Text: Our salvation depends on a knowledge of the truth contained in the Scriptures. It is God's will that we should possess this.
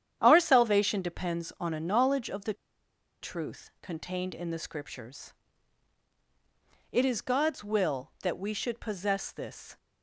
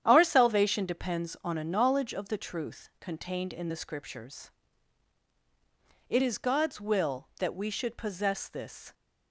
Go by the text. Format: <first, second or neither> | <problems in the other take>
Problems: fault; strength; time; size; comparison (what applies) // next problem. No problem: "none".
second | starts louder than the rest; strong; until 1.2 s; 9.5 dB; strong in the second // pauses between "the" and "truth"; noticeable; at 2.5 s; 0.68 s long